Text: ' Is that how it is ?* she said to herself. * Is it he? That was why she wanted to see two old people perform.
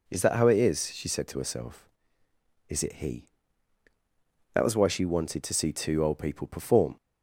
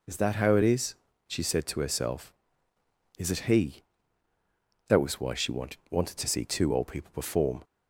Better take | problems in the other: first | says "wanted" twice; at 5.9 s

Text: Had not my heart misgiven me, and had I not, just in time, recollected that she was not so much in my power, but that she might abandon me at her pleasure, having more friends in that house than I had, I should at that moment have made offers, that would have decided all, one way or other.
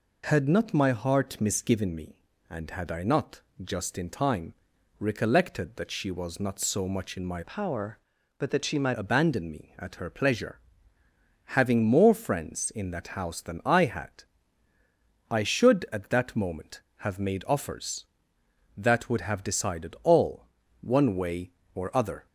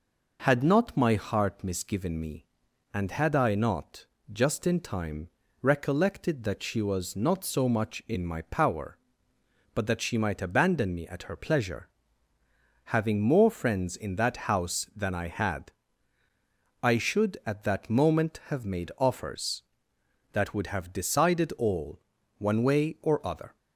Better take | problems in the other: second | changes voice from "power" to "might"; from 7.4 to 8.9 s; 1.5 s long

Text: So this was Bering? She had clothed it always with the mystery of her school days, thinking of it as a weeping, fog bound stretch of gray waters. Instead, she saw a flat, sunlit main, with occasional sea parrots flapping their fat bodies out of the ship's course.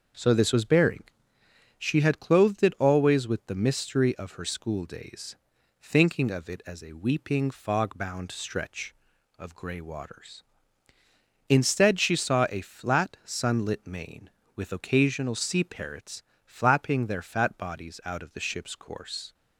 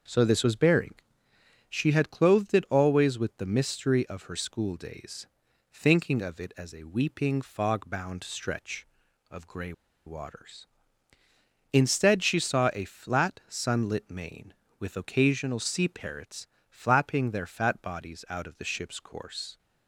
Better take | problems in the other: first | starts louder than the rest; until 1.8 s; 6.5 dB; also in the first // pauses between "gray" and "waters"; slight; at 9.7 s; 0.33 s long // pauses between "parrots" and "flapping"; slight; at 16.4 s; 0.24 s long; slight in the first

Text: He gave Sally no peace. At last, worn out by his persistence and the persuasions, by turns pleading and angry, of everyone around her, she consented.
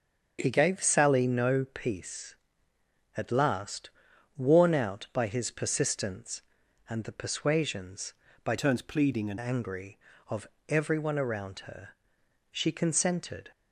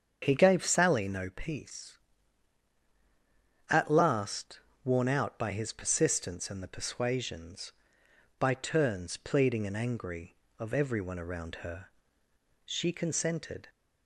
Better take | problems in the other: second | starts louder than the rest; until 1.4 s; 7 dB; strong in the second // changes voice from "turns" to "and"; from 8.5 to 9.3 s; 0.8 s long // pauses between "of" and "everyone"; slight; at 10.4 s; 0.22 s long

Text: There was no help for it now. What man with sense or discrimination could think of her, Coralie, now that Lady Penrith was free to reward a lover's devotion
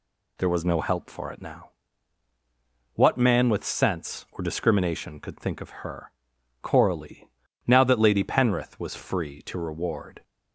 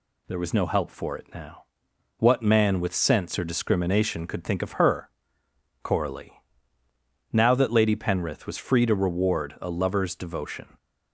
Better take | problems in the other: second | stops before "a lover's devotion"; at 10.2 s

